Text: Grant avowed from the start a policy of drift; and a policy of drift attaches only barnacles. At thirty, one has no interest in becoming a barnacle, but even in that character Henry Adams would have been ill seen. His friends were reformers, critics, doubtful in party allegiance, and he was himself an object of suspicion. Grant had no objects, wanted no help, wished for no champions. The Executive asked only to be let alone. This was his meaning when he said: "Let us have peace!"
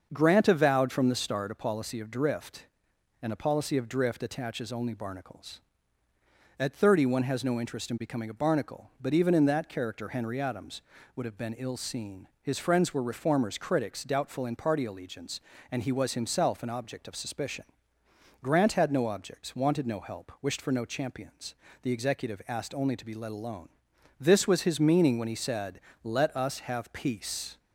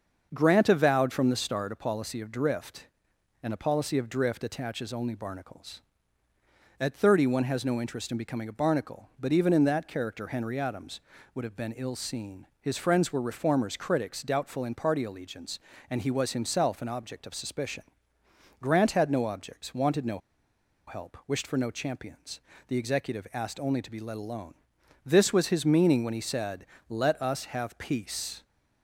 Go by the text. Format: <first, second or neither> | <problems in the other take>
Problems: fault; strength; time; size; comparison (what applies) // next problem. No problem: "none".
first | starts louder than the rest; until 1.3 s; 6.5 dB; also in the first // pauses between "no" and "help"; noticeable; at 20.1 s; 0.69 s long